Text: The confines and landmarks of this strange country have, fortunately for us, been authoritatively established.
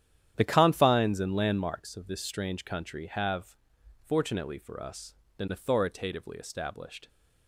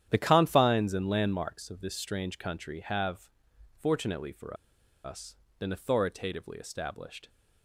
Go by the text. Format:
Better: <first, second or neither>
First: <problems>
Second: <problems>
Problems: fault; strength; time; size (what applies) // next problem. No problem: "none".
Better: first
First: starts louder than the rest; strong; until 1.3 s; 10.5 dB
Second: starts louder than the rest; strong; until 1.1 s; 10.5 dB // pauses between "for" and "us"; noticeable; at 4.5 s; 0.48 s long